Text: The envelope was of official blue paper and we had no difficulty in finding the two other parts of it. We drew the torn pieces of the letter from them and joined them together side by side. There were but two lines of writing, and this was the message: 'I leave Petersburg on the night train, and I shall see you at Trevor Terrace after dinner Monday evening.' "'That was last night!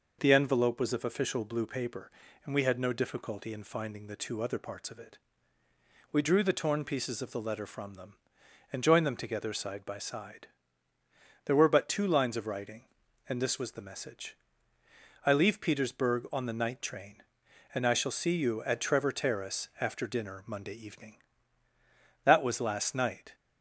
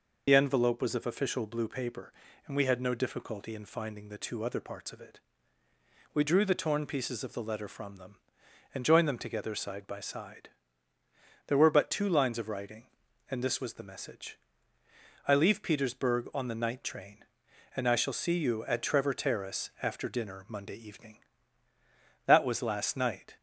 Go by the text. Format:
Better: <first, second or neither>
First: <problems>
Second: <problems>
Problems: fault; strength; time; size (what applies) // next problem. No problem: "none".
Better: first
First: none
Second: loses the start of "The"; at 0.2 s; 55 ms